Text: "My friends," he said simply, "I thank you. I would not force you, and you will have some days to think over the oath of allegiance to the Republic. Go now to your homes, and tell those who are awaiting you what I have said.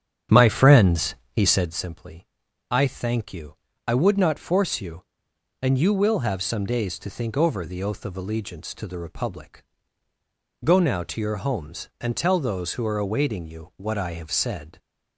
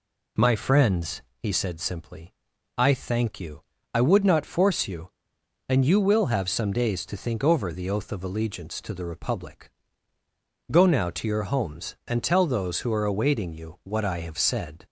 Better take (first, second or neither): second